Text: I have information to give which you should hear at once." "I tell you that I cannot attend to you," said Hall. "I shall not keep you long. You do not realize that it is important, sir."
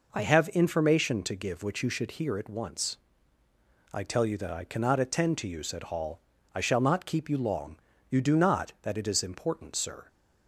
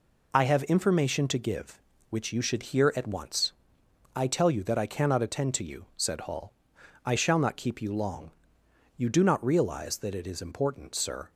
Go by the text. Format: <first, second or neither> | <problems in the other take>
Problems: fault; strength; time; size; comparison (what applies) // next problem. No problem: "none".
second | skips "realize"; at 8.7 s